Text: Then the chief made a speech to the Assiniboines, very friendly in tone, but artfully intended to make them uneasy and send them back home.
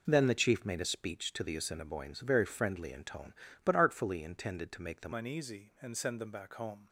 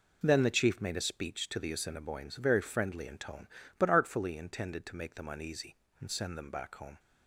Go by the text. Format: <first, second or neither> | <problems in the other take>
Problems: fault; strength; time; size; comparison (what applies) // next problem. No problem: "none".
second | changes voice at "uneasy"; from 5.1 s on; 1.7 s long